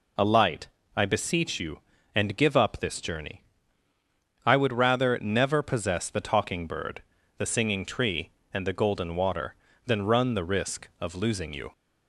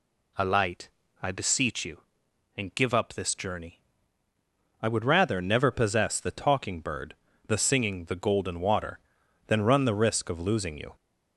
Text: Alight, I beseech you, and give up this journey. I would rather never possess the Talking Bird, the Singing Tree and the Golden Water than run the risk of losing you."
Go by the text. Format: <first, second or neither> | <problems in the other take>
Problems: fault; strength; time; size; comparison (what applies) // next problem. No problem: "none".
first | skips "Tree and"; at 8.0 s